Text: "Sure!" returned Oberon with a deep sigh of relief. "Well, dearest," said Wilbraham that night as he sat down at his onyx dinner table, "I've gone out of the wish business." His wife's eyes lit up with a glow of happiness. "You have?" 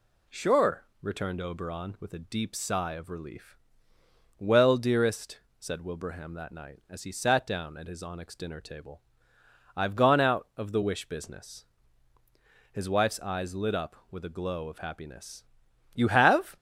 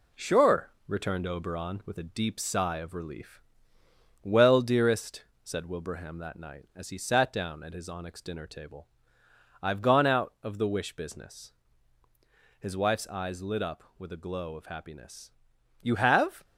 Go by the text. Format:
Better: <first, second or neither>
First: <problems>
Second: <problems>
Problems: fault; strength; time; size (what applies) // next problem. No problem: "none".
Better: first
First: none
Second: gets quieter; slight; throughout; 3.5 dB